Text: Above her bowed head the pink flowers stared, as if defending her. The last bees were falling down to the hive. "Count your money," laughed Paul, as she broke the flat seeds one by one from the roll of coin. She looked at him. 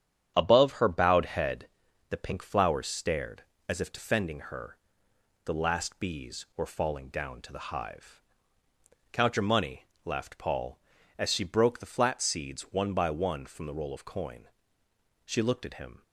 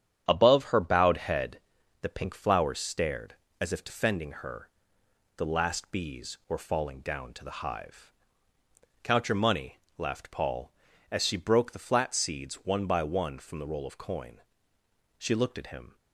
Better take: neither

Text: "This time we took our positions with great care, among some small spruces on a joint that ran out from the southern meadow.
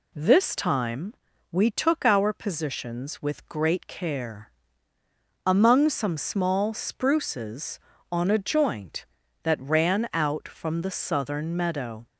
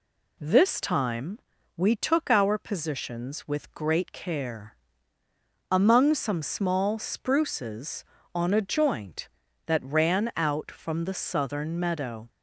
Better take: neither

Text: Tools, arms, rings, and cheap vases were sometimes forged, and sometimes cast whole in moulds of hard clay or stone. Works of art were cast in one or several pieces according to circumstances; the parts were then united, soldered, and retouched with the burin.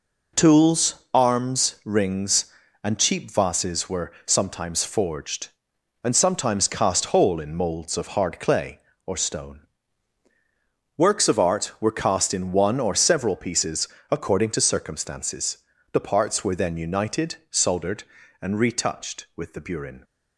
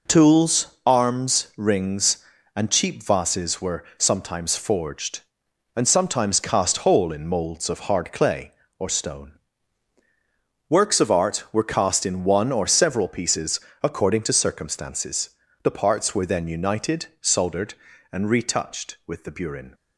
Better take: neither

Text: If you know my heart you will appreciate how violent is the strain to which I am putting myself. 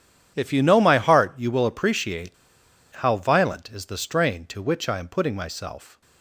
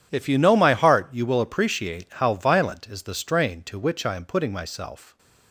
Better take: second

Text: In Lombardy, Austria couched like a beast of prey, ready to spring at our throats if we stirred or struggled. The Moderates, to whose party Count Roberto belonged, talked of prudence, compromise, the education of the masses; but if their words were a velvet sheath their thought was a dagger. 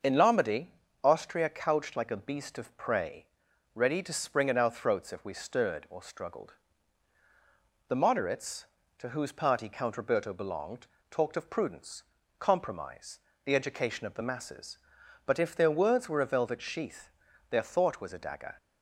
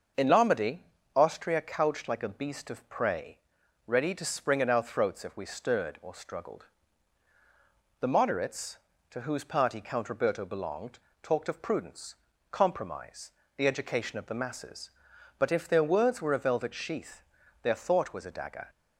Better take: neither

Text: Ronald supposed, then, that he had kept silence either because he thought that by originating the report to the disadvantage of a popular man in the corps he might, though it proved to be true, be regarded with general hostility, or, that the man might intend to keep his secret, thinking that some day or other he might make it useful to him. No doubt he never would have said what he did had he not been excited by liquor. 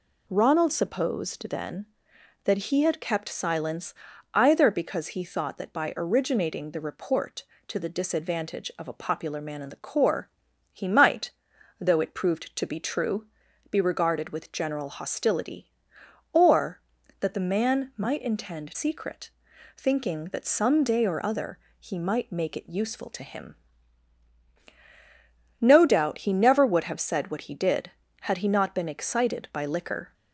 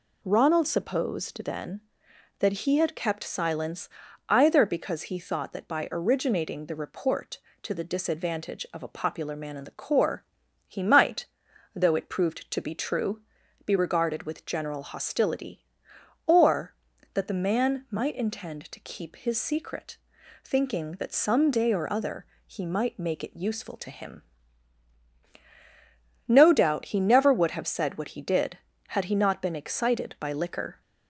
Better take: second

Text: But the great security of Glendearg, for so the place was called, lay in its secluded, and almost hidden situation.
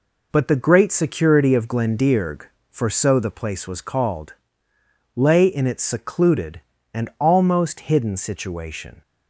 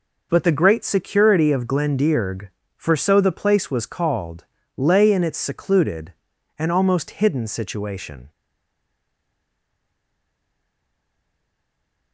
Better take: first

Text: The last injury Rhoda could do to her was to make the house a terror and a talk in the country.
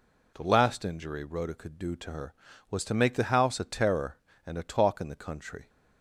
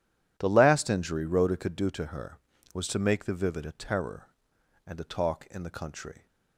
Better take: first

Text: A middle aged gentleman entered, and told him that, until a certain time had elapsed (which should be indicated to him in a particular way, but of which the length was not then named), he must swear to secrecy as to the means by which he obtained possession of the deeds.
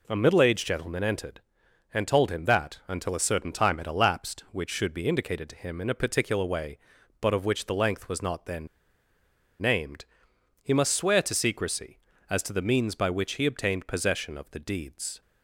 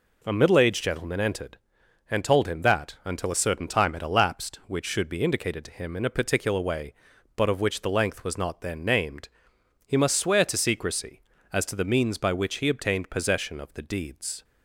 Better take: second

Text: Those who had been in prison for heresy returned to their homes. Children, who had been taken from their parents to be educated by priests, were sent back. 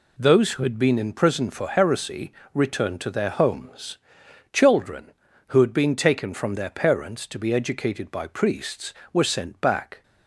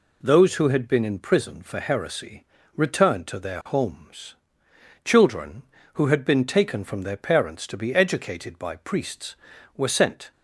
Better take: first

